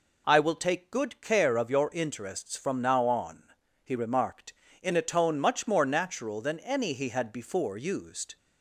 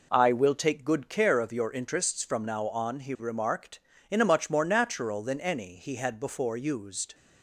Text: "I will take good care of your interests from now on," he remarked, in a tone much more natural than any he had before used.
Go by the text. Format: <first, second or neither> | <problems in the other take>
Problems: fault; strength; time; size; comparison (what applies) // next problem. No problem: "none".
first | skips "tone"; at 4.2 s